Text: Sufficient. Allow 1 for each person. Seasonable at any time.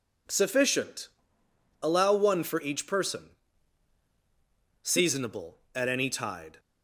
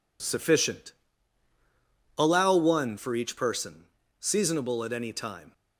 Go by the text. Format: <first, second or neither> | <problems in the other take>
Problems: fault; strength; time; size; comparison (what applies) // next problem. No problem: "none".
second | says "tide" for "time"; at 6.0 s